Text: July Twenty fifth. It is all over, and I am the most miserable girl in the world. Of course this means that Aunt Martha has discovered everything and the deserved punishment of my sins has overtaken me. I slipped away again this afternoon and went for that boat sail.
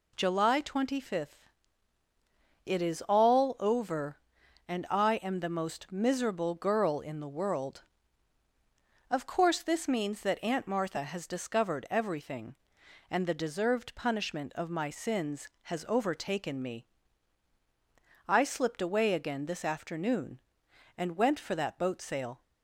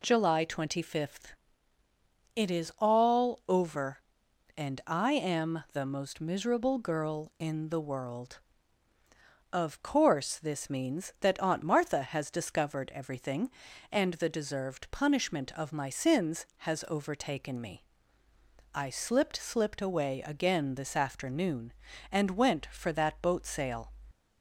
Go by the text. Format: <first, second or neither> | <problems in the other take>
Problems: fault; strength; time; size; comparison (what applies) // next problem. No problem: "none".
first | says "slipped" twice; at 19.3 s